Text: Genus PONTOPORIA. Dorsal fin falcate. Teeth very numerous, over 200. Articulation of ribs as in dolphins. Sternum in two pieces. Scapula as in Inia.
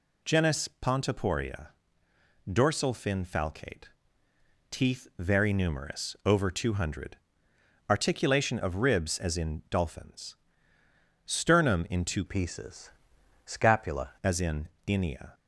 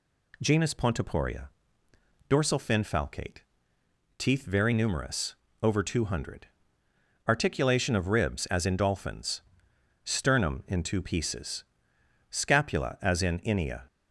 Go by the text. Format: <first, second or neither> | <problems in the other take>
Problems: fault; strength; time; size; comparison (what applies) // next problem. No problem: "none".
second | changes voice from "pieces" to "Scapula"; from 12.2 to 14.0 s; 1.8 s long // pauses between "in" and "Inia"; slight; at 14.6 s; 0.18 s long